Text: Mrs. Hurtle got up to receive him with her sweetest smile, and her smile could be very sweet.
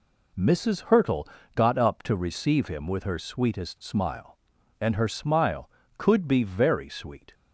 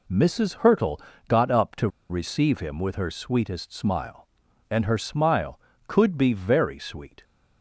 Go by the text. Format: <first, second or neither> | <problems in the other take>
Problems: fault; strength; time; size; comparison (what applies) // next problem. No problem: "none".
first | pauses between "Hurtle" and "got"; slight; at 0.9 s; 0.28 s long; slight in the first // pauses between "to" and "receive"; slight; at 1.8 s; 0.21 s long